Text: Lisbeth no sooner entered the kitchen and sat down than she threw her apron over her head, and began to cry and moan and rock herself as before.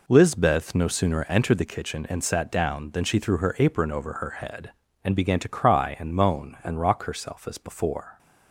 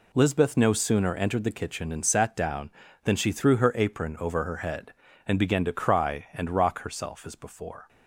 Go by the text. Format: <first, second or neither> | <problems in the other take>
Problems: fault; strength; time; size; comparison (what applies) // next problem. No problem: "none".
first | skips "and moan"; at 6.2 s